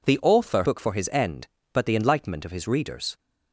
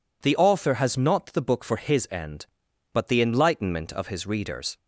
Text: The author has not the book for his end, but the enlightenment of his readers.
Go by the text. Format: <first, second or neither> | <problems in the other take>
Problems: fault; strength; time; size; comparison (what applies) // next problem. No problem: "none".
second | skips "has not the"; at 0.6 s